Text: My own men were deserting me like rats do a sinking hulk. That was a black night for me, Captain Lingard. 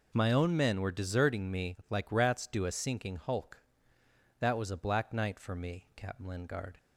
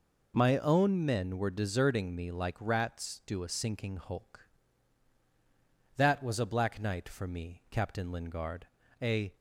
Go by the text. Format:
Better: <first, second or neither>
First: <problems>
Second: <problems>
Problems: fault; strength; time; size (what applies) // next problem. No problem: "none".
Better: first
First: none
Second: goes on to say "A"; slight; from 9.0 s on; 0.34 s long